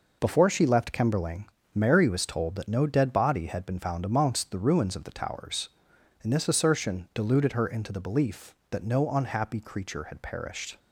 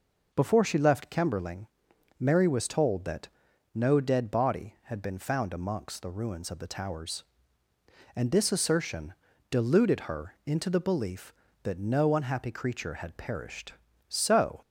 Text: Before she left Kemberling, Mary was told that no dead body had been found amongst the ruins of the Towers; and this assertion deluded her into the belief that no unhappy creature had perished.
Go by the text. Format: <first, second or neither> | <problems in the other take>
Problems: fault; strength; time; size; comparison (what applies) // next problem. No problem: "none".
first | pauses between "that" and "no"; noticeable; at 3.2 s; 0.48 s long // pauses between "assertion" and "deluded"; slight; at 9.1 s; 0.36 s long // goes on to say "So"; from 14.0 s on; 0.54 s long